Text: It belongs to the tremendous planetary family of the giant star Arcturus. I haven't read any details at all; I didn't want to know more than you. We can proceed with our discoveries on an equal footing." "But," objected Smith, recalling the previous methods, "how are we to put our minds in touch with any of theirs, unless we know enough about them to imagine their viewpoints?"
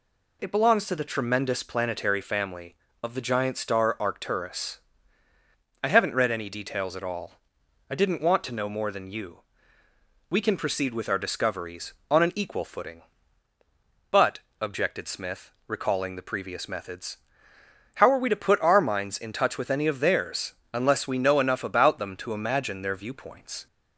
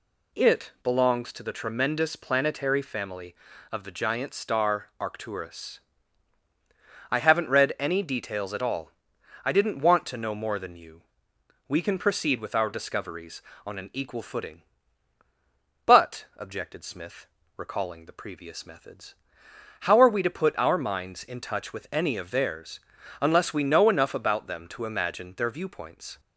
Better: neither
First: none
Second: none

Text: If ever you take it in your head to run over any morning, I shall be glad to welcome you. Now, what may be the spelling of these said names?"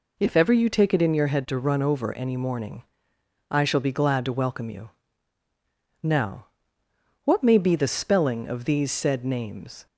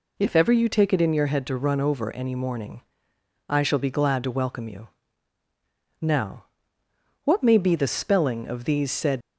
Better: first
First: none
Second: stops before "names"; at 9.2 s

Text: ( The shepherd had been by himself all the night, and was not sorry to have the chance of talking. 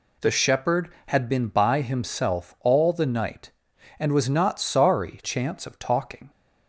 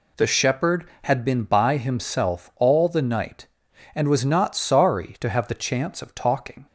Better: second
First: skips "to have the"; at 5.2 s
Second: none

